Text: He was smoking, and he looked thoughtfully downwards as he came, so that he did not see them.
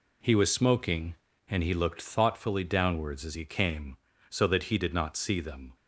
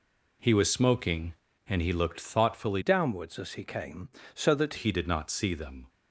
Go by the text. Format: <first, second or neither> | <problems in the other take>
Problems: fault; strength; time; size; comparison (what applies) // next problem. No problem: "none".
first | changes voice from "downwards" to "that"; from 2.8 to 4.7 s; 1.9 s long